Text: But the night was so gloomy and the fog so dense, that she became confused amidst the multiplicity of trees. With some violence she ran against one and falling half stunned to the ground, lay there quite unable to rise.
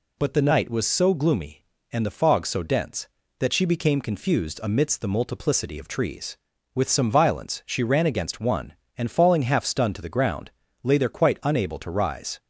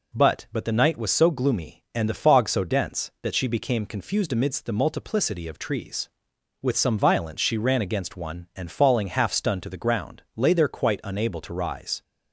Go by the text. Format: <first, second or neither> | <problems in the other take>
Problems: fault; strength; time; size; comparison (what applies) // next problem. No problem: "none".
first | says "But" twice; at 0.5 s